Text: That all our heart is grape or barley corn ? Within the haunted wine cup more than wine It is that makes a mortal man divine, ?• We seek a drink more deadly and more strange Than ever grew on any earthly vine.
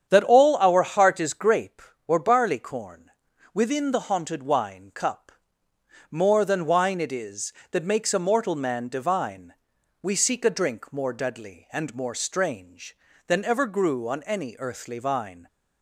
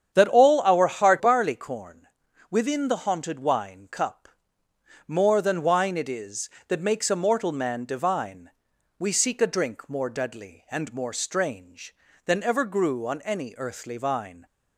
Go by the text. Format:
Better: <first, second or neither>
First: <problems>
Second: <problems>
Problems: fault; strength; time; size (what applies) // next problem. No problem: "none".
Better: first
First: starts louder than the rest; strong; until 1.1 s; 8.5 dB // pauses between "cup" and "more"; noticeable; at 5.3 s; 0.80 s long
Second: starts louder than the rest; strong; until 1.1 s; 8.5 dB // skips "is grape or"; at 1.1 s // pauses between "cup" and "more"; noticeable; at 4.2 s; 0.80 s long